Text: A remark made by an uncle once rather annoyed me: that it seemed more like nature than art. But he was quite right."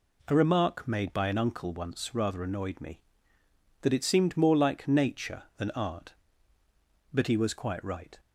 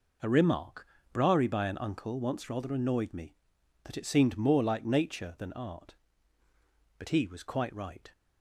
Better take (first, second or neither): first